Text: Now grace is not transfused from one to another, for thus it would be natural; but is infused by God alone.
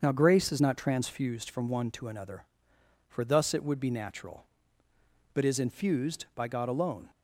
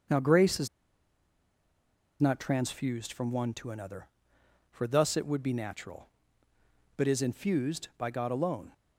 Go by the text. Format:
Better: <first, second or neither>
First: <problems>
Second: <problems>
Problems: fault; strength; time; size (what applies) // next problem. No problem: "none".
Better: first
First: starts louder than the rest; until 1.0 s; 7 dB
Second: starts louder than the rest; until 2.6 s; 6.5 dB // pauses between "is" and "not"; strong; at 0.6 s; 1.5 s long